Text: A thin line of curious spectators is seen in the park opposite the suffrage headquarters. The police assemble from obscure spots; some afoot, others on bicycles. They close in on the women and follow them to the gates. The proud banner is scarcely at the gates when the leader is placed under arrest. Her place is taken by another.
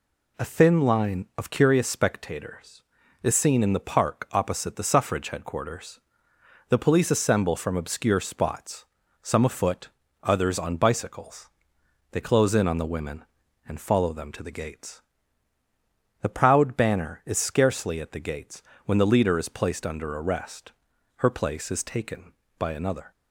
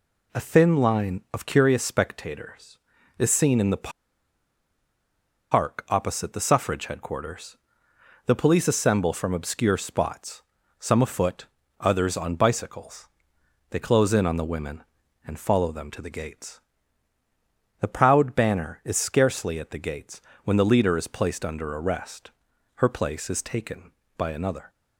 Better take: first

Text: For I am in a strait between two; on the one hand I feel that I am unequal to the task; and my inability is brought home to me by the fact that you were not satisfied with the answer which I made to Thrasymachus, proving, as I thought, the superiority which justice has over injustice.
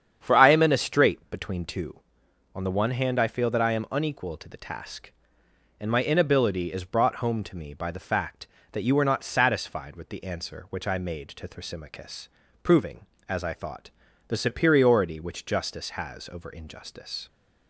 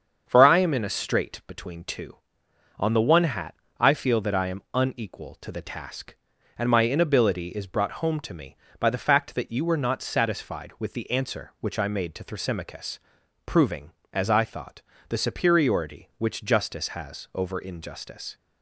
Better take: first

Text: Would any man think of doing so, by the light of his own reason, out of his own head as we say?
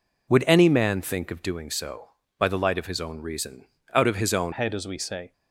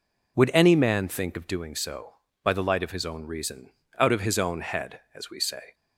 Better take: second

